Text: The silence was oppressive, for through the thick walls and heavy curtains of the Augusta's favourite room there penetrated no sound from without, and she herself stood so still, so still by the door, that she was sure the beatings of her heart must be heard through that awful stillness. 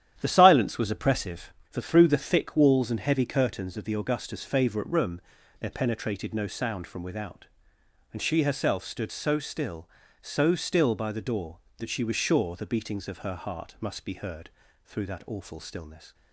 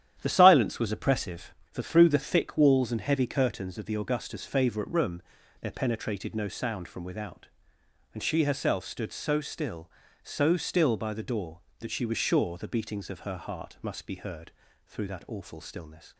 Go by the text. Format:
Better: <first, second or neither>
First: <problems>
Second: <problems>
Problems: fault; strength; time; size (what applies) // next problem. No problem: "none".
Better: neither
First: starts louder than the rest; strong; until 1.2 s; 10.5 dB // pauses between "room" and "there"; at 5.2 s; 0.38 s long // pauses between "heard" and "through"; at 14.4 s; 0.38 s long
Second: starts louder than the rest; strong; until 1.2 s; 10.5 dB // pauses between "room" and "there"; at 5.2 s; 0.38 s long // pauses between "heard" and "through"; at 14.4 s; 0.38 s long